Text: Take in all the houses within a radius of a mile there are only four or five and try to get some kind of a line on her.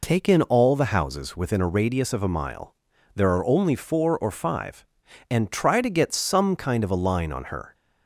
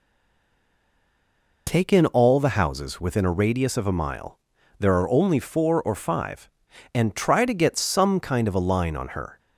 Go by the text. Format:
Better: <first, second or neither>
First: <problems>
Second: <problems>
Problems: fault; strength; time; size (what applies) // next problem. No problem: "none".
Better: first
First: pauses between "mile" and "there"; at 2.7 s; 0.42 s long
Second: stays silent before the first word; noticeable; until 1.6 s; 1.6 s long // pauses between "mile" and "there"; at 4.3 s; 0.42 s long